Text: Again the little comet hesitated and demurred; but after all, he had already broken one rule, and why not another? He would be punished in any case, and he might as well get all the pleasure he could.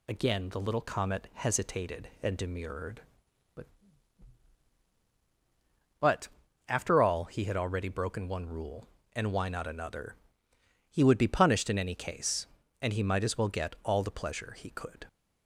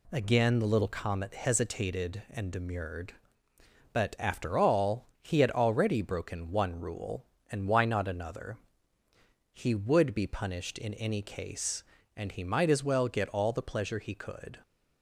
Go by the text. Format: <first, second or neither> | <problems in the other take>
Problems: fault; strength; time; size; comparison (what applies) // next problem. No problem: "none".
second | says "but" twice; at 6.0 s